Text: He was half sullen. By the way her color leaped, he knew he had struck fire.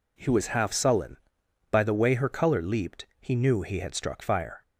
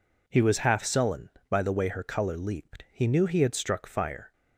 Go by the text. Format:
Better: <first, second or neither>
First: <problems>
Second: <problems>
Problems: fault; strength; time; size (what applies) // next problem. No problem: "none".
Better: neither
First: none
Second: none